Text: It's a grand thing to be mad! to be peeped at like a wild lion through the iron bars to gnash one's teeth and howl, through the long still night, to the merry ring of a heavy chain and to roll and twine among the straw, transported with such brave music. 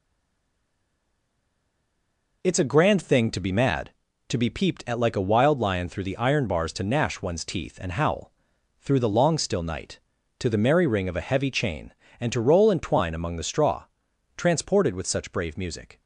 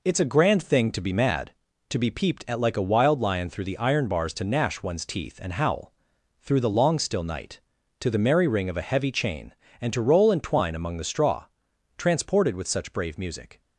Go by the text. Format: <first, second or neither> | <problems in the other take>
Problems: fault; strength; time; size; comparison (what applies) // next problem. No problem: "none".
second | stays silent before the first word; until 2.4 s; 2.4 s long